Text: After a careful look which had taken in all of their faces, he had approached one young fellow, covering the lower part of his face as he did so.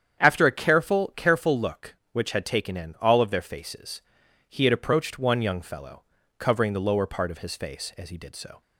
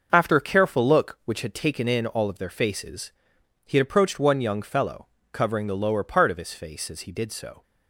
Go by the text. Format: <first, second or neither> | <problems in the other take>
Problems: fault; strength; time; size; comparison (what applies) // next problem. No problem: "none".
second | starts louder than the rest; strong; until 1.2 s; 8.5 dB; noticeable in the second // says "careful" twice; at 1.1 s